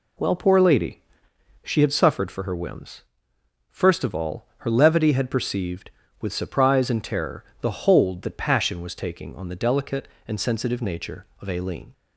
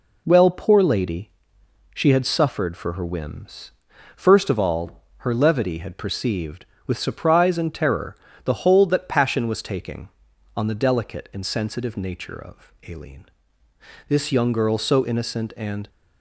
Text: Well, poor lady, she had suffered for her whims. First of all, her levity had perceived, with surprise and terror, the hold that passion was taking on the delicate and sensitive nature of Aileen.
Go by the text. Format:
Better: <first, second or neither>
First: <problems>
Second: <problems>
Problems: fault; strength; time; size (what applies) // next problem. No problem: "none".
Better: first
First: none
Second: pauses between "of" and "Aileen"; slight; at 12.7 s; 0.16 s long // goes on to say "This young girl so innocent and"; strong; from 14.0 s on; 1.8 s long